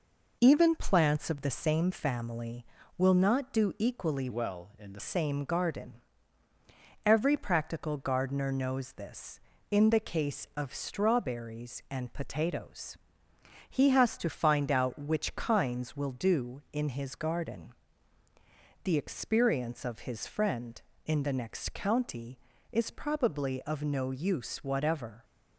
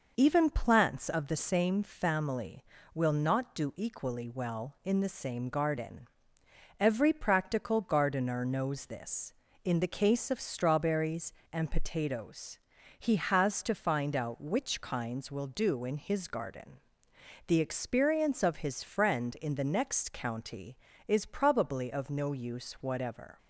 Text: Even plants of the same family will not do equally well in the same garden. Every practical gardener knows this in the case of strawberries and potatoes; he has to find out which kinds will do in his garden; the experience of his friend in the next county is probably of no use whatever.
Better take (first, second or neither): second